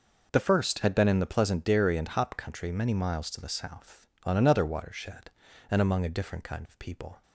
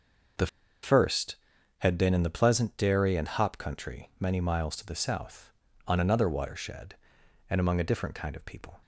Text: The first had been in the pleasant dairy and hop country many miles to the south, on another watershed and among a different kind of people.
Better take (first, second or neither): first